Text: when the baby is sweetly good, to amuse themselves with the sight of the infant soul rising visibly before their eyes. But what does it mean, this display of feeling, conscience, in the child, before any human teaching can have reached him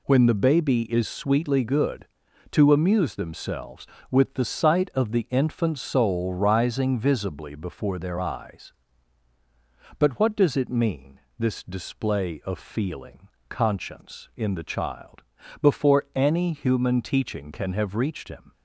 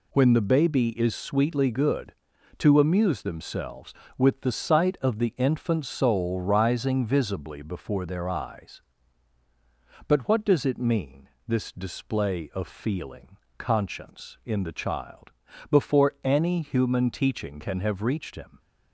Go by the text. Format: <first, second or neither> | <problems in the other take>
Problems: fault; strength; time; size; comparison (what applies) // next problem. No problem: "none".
neither | none